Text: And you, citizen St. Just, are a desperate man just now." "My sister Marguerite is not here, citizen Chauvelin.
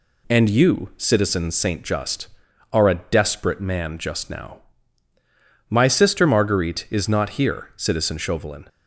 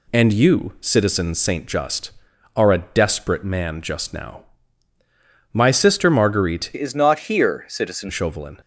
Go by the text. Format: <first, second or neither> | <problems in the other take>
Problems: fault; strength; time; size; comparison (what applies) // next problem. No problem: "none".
first | changes voice from "is" to "citizen"; from 6.7 to 8.0 s; 1.3 s long